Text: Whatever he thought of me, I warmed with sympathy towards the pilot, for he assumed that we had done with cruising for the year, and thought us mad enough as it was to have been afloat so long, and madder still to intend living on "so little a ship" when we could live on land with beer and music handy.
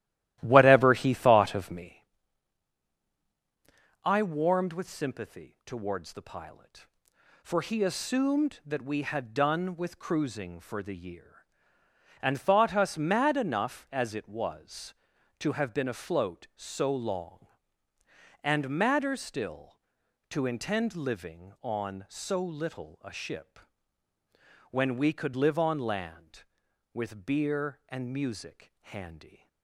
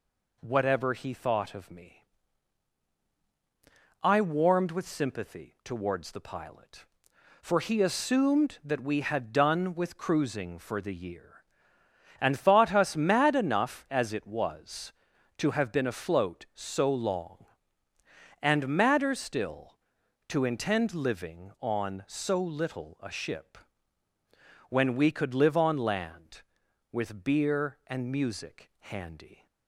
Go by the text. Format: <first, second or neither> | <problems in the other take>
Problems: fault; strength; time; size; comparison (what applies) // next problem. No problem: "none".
second | starts louder than the rest; strong; until 2.1 s; 14 dB // pauses between "ship" and "when"; at 23.5 s; 1.1 s long; also in the second